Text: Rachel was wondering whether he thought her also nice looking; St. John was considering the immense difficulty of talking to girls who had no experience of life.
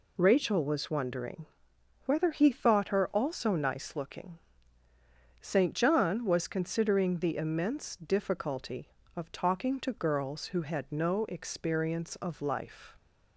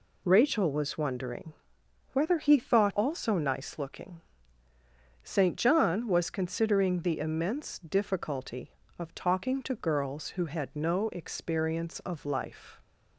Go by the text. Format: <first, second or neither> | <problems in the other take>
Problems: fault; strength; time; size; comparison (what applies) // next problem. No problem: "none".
first | pauses between "wondering" and "whether"; noticeable; at 1.5 s; 0.62 s long; noticeable in the first // skips "her"; at 2.9 s